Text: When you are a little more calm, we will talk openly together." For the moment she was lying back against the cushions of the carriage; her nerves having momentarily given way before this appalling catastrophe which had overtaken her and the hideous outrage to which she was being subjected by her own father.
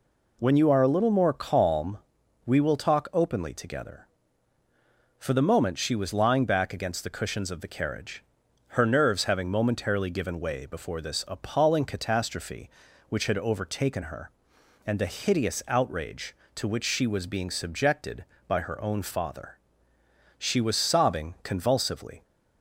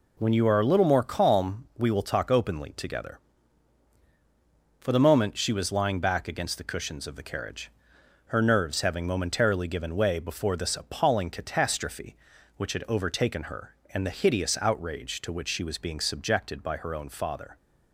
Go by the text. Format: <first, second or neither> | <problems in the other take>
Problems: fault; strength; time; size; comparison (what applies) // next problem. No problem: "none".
second | goes on to say "She was sobbing convulsively"; strong; from 20.3 s on; 1.8 s long